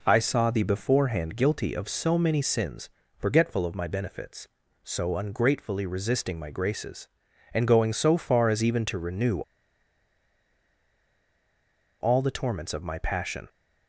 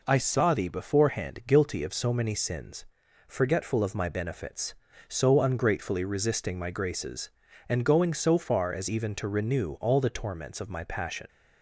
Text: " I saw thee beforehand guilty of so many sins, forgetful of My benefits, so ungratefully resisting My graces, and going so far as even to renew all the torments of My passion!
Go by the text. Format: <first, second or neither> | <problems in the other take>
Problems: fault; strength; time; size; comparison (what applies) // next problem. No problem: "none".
second | pauses between "renew" and "all"; strong; at 9.4 s; 2.5 s long